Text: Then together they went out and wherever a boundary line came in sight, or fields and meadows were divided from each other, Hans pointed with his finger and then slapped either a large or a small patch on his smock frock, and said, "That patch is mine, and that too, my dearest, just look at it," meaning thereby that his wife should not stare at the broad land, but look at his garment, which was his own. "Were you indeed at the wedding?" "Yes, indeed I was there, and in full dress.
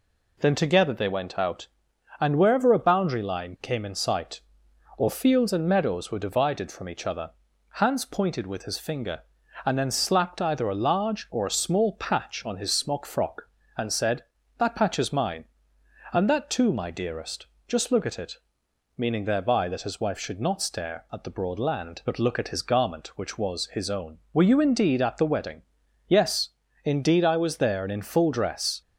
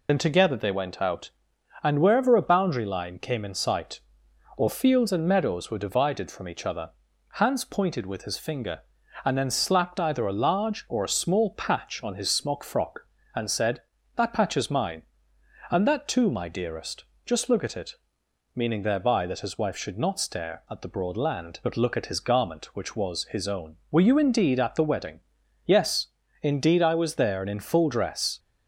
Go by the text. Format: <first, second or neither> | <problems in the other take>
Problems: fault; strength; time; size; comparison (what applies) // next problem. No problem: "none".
first | loses the start of "Then"; at 0.0 s; 70 ms